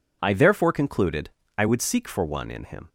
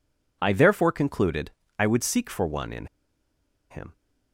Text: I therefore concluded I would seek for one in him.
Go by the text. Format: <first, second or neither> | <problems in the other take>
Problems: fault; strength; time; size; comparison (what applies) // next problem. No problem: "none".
first | pauses between "concluded" and "I"; slight; at 1.5 s; 0.30 s long; slight in the first // pauses between "in" and "him"; noticeable; at 2.8 s; 0.84 s long